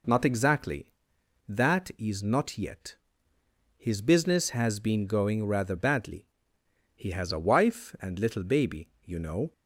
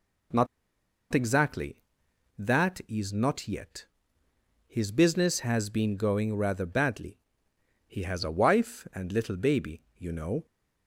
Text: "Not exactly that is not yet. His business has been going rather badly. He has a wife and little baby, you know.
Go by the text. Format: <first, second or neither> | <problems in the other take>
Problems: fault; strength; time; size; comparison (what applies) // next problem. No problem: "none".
first | pauses between "Not" and "exactly"; noticeable; at 0.4 s; 0.66 s long